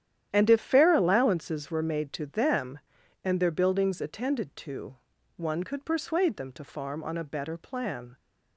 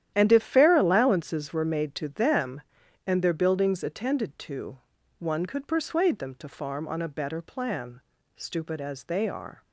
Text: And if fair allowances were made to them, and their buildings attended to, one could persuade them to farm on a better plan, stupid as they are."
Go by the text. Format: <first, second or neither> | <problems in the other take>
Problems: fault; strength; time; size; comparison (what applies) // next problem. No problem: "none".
second | starts louder than the rest; strong; until 1.3 s; 10.5 dB; strong in the second // stops before "stupid as they are"; at 8.1 s